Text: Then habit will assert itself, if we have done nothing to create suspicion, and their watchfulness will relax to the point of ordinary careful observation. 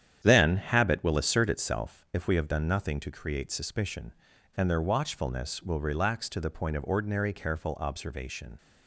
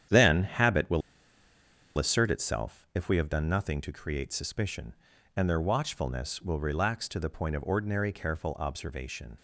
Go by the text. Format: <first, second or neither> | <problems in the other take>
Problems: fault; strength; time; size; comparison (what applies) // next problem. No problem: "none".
first | starts louder than the rest; strong; until 2.0 s; 9.5 dB; strong in the first // pauses between "will" and "assert"; noticeable; at 1.0 s; 0.97 s long